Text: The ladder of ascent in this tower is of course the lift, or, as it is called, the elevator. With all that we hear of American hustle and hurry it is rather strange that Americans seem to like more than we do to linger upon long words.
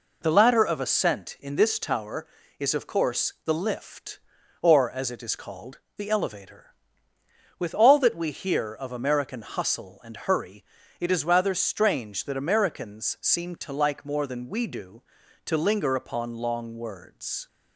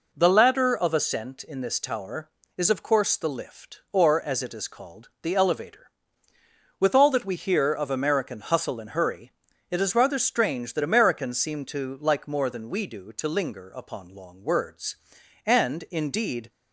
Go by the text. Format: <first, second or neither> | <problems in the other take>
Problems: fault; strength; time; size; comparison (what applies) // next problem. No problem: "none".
first | pauses between "hurry" and "it"; at 9.3 s; 0.38 s long; slight in the first // goes on to say "And indeed"; noticeable; from 15.4 s on; 1.0 s long